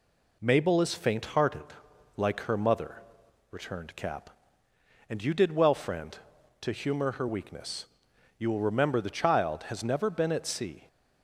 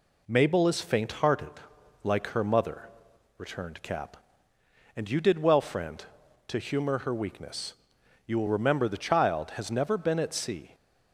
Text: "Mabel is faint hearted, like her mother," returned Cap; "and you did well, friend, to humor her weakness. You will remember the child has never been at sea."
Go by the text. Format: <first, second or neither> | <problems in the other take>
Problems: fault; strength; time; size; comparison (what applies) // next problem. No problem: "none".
neither | none